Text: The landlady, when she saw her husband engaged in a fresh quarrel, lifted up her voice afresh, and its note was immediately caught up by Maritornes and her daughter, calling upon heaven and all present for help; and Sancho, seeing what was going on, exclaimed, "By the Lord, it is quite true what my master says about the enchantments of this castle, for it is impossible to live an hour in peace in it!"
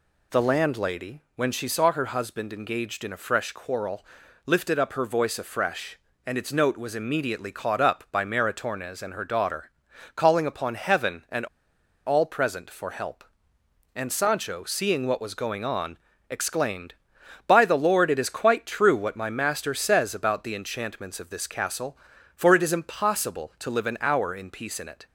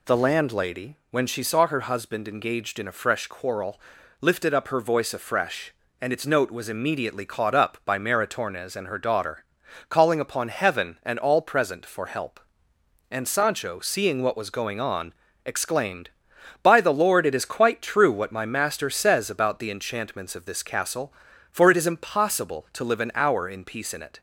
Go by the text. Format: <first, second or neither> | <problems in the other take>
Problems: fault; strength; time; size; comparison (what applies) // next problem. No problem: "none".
second | pauses between "and" and "all"; noticeable; at 11.4 s; 0.61 s long